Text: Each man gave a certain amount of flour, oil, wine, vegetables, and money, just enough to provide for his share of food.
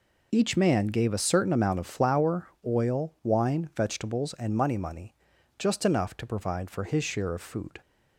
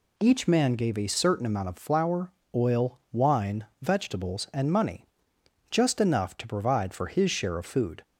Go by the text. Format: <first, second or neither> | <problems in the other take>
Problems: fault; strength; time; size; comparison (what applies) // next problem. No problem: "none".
second | says "money" twice; at 4.7 s